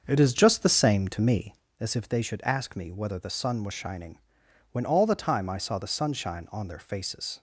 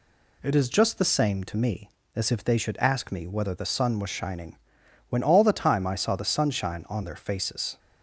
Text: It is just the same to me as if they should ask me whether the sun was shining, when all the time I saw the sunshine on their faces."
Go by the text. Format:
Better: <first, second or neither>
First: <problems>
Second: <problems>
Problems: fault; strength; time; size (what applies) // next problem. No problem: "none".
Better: second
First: starts louder than the rest; until 1.7 s; 6.5 dB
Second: none